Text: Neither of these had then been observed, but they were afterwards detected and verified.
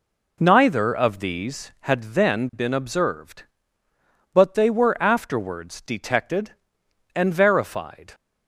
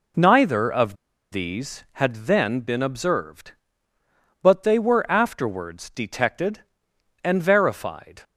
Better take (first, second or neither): first